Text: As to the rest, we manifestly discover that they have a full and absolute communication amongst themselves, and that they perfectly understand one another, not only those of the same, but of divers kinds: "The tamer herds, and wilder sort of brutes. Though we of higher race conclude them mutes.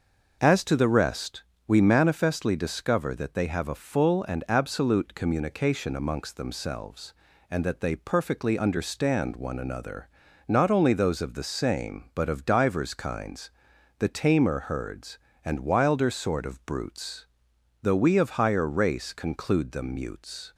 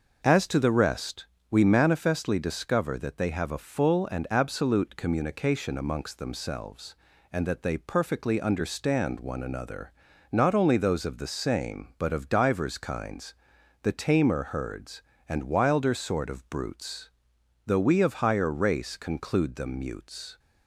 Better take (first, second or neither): neither